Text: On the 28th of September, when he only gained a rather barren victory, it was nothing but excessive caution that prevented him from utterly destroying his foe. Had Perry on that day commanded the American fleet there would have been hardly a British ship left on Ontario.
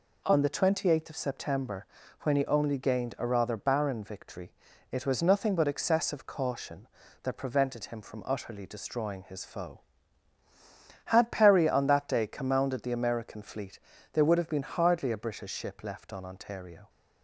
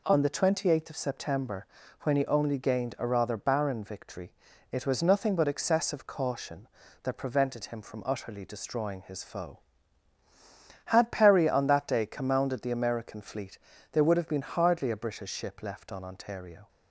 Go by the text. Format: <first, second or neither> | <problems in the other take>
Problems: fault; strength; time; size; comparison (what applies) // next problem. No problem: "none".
neither | pauses between "fleet" and "there"; slight; the same in both